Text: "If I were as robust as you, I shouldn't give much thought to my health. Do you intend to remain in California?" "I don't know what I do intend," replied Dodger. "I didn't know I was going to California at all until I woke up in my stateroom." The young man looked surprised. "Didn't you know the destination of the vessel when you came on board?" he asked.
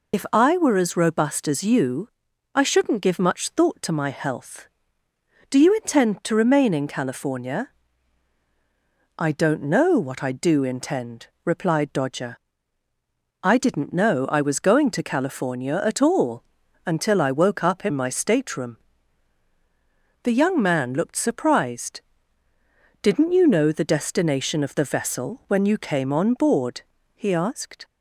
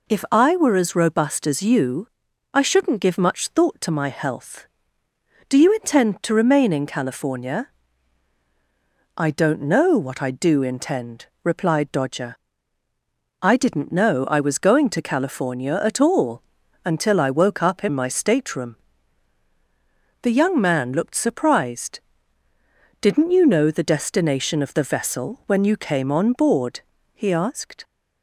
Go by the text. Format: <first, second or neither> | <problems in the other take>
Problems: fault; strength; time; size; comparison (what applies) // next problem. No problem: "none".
second | loses the start of "If"; at 0.1 s; 40 ms // pauses between "all" and "until"; at 16.4 s; 0.42 s long; also in the second